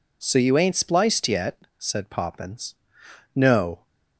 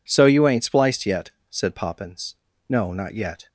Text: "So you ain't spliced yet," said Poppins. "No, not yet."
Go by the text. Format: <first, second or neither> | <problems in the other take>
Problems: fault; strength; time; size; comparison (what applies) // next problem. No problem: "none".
second | stops before "not yet"; at 3.8 s